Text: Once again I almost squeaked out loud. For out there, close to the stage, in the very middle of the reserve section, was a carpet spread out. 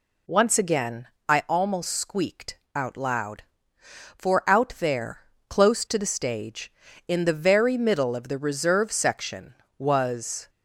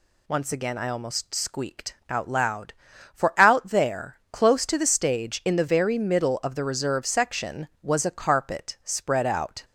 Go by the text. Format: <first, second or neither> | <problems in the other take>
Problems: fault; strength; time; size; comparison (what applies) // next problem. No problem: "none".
second | pauses between "again" and "I"; slight; at 1.0 s; 0.22 s long // pauses between "squeaked" and "out"; slight; at 2.5 s; 0.18 s long // stops before "a carpet spread out"; at 10.4 s